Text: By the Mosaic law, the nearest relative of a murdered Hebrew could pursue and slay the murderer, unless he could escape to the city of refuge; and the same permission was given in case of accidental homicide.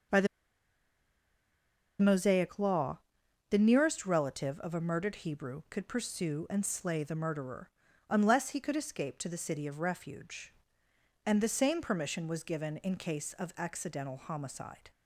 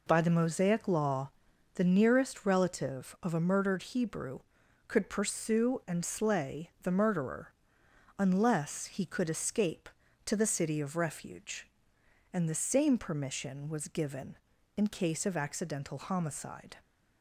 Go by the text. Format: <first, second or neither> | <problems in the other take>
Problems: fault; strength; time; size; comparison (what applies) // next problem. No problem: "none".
second | starts louder than the rest; noticeable; until 2.8 s; 6 dB // pauses between "the" and "Mosaic"; strong; at 0.2 s; 1.7 s long